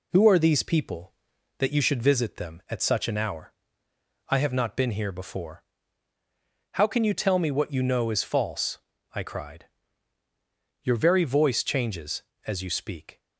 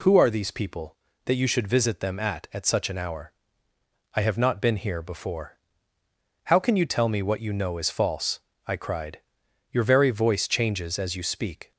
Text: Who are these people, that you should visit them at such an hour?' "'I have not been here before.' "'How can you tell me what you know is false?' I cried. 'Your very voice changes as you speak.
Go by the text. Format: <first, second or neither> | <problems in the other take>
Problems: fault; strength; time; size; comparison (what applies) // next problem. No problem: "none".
first | says "at" twice; at 2.5 s